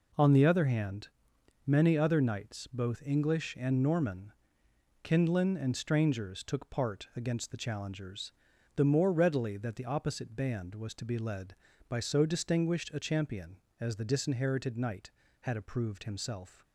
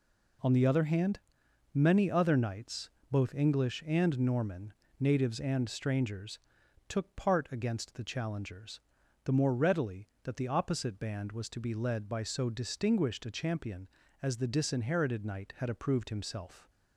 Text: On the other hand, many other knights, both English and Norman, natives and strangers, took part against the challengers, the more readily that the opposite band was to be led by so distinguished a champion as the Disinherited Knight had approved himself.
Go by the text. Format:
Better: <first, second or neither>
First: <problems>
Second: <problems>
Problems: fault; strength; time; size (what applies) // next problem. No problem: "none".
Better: second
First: says "kindlin" for "natives"; at 5.0 s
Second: none